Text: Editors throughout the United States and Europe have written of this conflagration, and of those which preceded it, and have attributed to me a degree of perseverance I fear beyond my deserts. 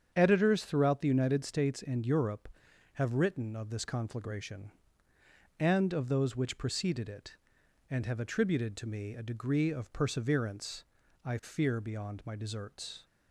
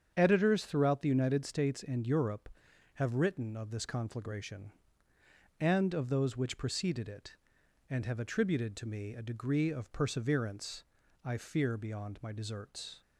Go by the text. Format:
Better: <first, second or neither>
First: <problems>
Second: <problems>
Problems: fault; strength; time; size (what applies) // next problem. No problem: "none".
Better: neither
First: starts louder than the rest; strong; until 1.1 s; 8 dB // pauses between "perseverance" and "I"; at 10.8 s; 0.40 s long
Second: starts louder than the rest; strong; until 1.1 s; 8 dB // pauses between "perseverance" and "I"; at 10.8 s; 0.40 s long